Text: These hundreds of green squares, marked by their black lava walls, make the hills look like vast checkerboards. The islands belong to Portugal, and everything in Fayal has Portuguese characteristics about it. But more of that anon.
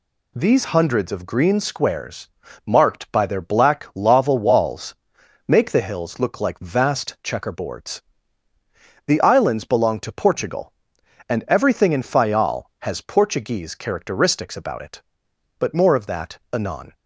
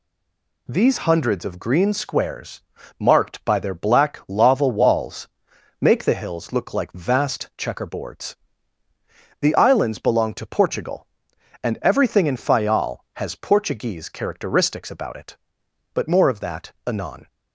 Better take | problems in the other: first | stays silent before the first word; slight; until 0.6 s; 0.6 s long

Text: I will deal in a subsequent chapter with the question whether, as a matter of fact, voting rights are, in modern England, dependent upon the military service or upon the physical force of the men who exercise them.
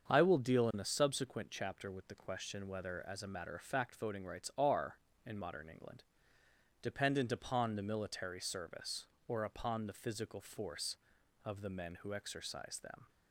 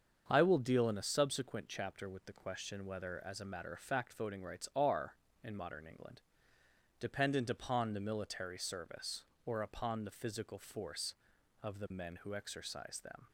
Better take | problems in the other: neither | starts louder than the rest; the same in both

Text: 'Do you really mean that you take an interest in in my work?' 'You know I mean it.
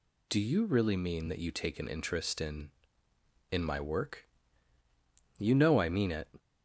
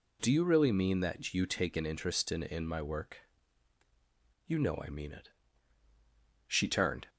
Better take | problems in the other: first | goes on to say "She turned"; noticeable; from 6.4 s on; 0.64 s long

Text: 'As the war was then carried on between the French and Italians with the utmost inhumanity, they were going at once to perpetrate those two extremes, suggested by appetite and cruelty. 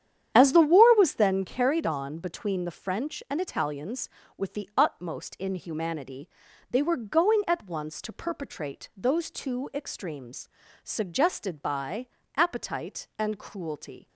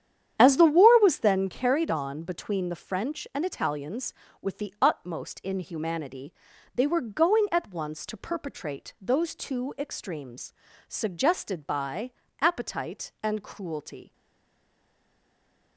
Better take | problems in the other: first | starts louder than the rest; strong; until 1.4 s; 9.5 dB; strong in the first // pauses between "by" and "appetite"; slight; at 12.1 s; 0.30 s long; slight in the first // stays silent after the last word; noticeable; from 14.1 s on; 1.6 s long

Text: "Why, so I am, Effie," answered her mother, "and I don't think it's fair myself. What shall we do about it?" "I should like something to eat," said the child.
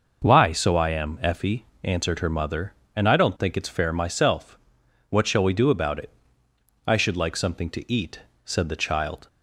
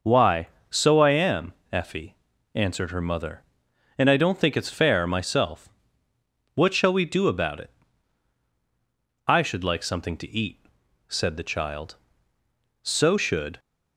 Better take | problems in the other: first | goes on to say "So should"; noticeable; from 12.8 s on; 0.76 s long

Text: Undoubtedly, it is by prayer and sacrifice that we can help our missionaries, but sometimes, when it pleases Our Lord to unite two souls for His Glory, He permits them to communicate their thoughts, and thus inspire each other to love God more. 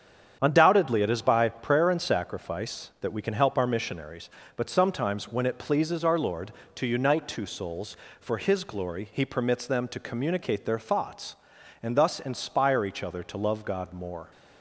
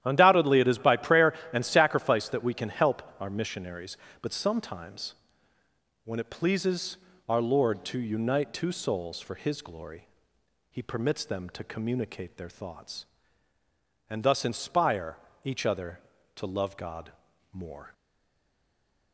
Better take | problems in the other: first | starts louder than the rest; strong; until 1.0 s; 11.5 dB; strong in the first // pauses between "help" and "our"; slight; at 3.0 s; 0.16 s long // pauses between "pleases" and "Our"; slight; at 6.9 s; 0.32 s long // pauses between "inspire" and "each"; slight; at 15.1 s; 0.28 s long // pauses between "God" and "more"; at 17.1 s; 0.42 s long // stays silent after the last word; noticeable; from 17.9 s on; 1.2 s long

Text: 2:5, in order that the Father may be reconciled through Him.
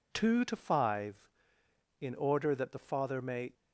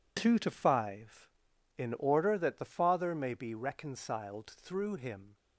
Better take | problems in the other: second | stops before "be reconciled through Him"; at 3.5 s

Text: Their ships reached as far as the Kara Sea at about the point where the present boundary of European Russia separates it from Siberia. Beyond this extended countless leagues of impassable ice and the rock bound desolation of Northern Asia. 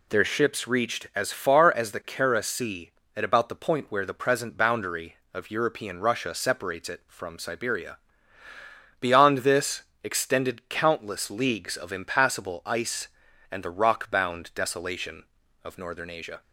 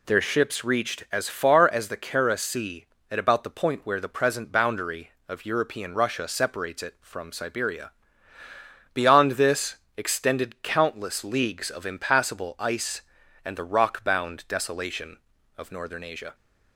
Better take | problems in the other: neither | pauses between "this" and "extended"; slight; the same in both

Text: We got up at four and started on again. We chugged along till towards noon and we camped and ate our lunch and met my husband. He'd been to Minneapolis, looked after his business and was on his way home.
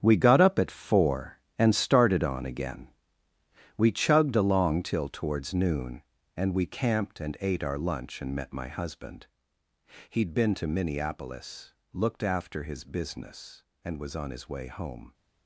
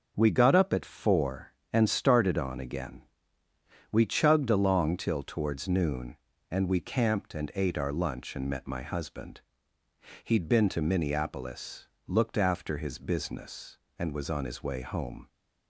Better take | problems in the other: second | gets quieter; strong; throughout; 13 dB // starts louder than the rest; strong; until 1.0 s; 9.5 dB; strong in the second

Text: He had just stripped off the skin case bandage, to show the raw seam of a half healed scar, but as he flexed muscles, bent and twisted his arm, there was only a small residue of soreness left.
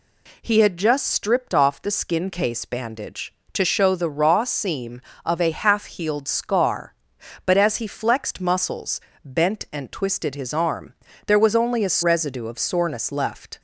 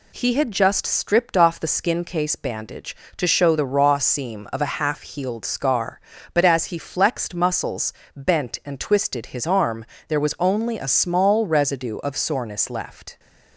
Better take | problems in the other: second | skips "small"; at 12.0 s

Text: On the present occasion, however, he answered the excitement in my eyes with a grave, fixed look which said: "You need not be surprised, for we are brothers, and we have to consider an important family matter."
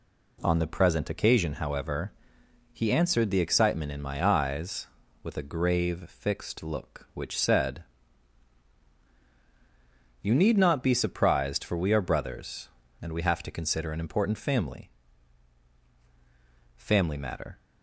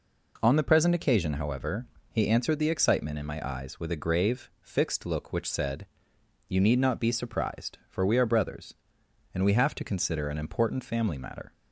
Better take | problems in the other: second | says "family" twice; at 16.7 s

